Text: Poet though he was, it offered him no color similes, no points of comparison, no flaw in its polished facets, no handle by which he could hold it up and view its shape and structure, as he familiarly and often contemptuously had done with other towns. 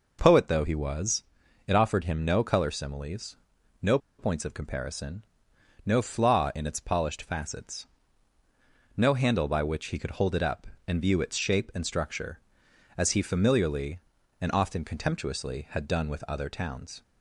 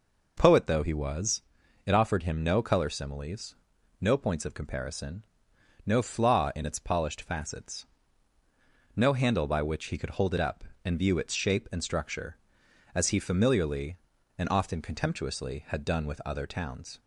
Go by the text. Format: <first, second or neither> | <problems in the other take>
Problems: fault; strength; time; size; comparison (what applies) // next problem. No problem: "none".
second | pauses between "no" and "points"; slight; at 3.9 s; 0.21 s long